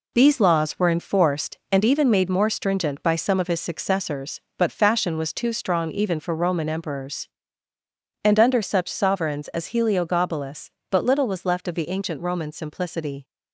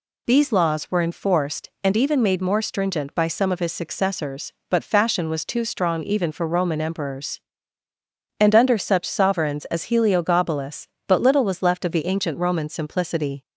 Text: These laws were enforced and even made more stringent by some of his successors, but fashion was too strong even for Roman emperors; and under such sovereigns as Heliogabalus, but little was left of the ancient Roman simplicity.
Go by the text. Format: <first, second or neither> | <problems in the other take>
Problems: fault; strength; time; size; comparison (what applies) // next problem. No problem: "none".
second | gets quieter; throughout; 7 dB